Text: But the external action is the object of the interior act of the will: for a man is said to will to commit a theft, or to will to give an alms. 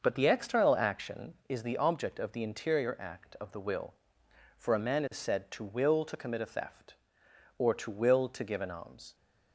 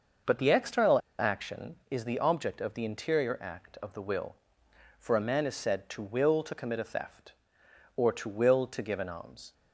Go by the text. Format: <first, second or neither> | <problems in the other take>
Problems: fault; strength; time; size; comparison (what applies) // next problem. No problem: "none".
first | starts louder than the rest; noticeable; until 1.4 s; 6 dB; noticeable in the first // pauses between "external" and "action"; slight; at 0.9 s; 0.20 s long